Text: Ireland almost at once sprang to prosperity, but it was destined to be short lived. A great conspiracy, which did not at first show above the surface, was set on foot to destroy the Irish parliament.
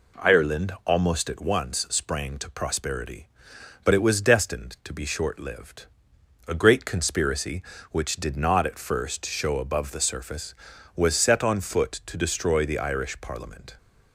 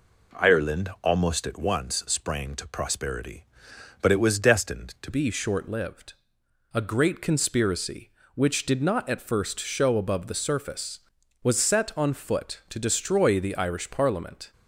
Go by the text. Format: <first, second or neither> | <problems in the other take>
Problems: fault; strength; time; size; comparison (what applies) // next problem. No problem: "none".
first | changes voice at "be"; from 5.1 s on; 9.4 s long